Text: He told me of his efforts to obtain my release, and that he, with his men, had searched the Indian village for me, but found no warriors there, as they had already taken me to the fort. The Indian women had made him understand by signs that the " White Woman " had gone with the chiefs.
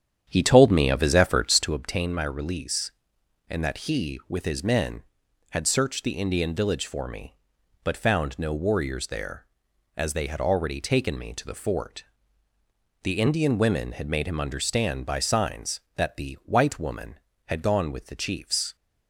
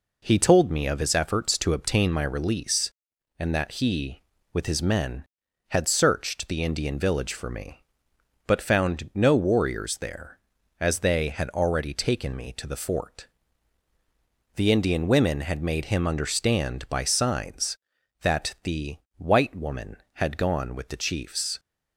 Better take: second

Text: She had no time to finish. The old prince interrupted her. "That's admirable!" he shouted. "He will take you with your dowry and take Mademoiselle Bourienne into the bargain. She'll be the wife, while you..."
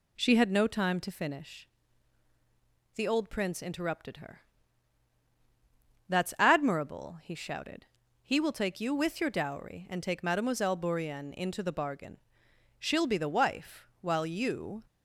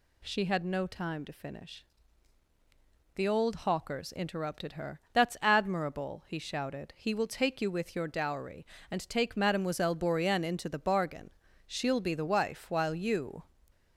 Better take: first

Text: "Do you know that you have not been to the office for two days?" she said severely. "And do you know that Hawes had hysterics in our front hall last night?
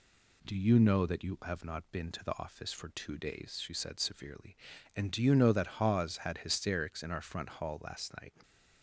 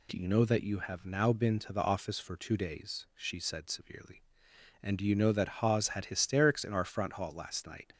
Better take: first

